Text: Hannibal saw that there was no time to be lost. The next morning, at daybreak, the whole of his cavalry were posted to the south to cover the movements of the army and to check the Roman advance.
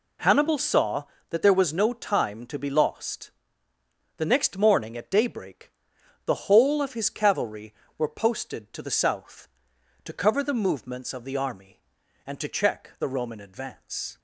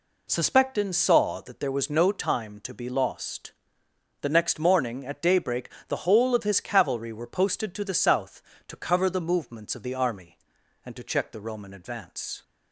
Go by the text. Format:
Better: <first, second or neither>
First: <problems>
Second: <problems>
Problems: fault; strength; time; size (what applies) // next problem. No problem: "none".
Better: first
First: none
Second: says "Suspectin" for "Hannibal"; at 0.2 s